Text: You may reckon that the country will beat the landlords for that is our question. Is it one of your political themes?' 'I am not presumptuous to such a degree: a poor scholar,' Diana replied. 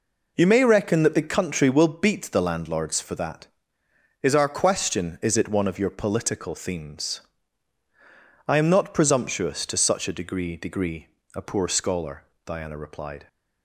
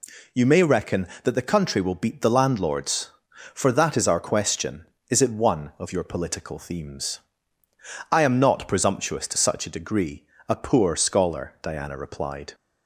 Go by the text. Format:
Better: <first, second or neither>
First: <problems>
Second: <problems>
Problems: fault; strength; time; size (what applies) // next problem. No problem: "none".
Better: second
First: says "degree" twice; at 10.5 s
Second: none